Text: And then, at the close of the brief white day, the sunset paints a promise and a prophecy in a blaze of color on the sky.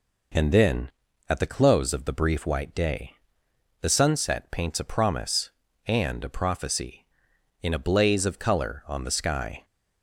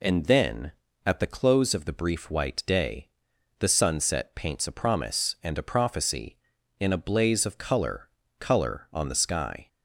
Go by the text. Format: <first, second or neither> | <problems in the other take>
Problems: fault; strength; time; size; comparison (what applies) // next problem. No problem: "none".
first | says "color" twice; at 8.3 s